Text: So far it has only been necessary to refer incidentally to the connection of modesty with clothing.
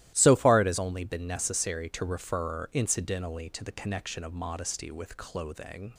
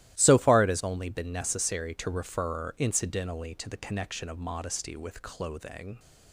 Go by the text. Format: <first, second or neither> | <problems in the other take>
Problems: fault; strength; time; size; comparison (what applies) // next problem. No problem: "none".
neither | starts louder than the rest; strong; the same in both